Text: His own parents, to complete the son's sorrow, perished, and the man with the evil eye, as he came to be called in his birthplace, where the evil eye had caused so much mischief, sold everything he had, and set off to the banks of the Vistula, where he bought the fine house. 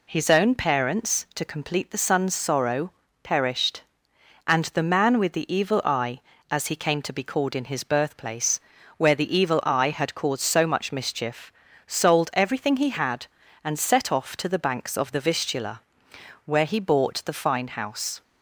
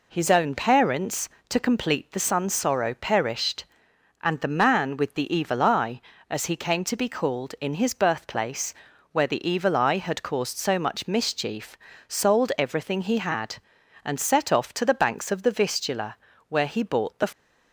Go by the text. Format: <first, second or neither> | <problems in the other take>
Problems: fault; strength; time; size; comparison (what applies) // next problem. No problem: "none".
first | stops before "fine house"; at 17.3 s